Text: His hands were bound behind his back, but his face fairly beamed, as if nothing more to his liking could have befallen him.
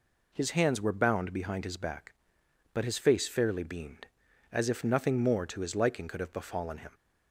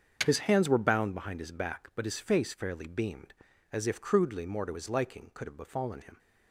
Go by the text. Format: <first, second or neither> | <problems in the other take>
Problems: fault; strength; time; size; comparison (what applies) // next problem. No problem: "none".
first | starts louder than the rest; until 1.2 s; 6.5 dB // says "crudely" for "nothing"; at 4.0 s